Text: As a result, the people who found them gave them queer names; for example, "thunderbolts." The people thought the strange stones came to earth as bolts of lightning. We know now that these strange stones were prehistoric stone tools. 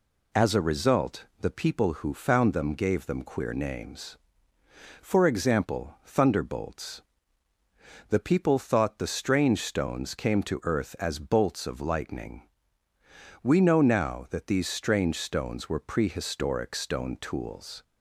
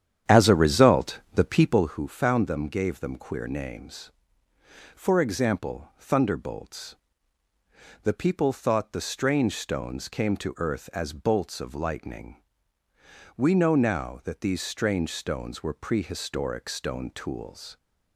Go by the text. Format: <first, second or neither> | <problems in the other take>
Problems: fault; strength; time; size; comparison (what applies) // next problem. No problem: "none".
first | starts louder than the rest; strong; until 2.0 s; 9.5 dB